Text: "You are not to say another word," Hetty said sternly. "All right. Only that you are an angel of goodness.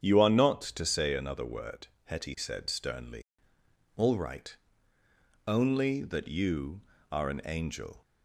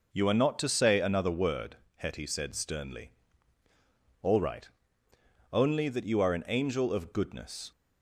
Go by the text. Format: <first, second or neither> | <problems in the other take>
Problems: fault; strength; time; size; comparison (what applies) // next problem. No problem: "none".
second | starts louder than the rest; strong; until 1.0 s; 8 dB // stops before "of goodness"; at 8.0 s